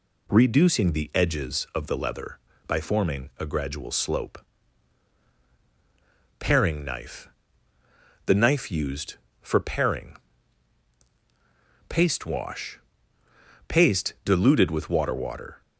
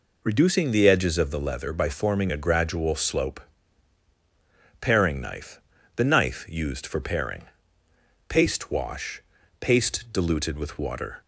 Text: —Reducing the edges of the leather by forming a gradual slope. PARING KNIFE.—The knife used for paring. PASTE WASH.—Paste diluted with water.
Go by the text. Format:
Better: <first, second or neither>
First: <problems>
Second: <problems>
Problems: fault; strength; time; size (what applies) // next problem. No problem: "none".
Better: second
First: says "water" twice; at 15.1 s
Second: none